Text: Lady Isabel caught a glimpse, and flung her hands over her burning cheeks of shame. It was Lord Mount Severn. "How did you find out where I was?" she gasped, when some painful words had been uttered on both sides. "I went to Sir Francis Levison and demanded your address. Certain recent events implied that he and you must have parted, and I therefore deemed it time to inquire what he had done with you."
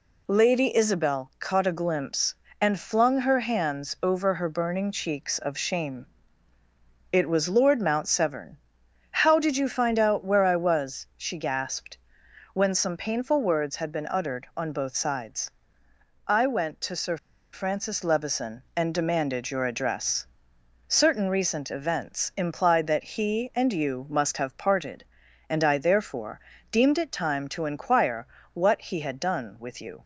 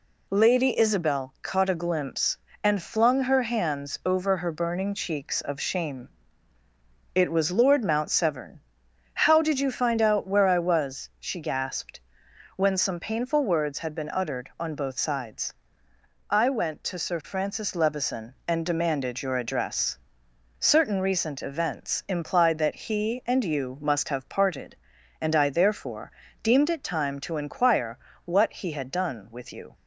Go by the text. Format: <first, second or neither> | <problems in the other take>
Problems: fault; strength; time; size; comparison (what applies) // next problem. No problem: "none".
second | pauses between "Sir" and "Francis"; slight; at 17.1 s; 0.34 s long // pauses between "therefore" and "deemed"; slight; at 26.4 s; 0.32 s long; slight in the second // pauses between "inquire" and "what"; slight; at 28.2 s; 0.26 s long; slight in the second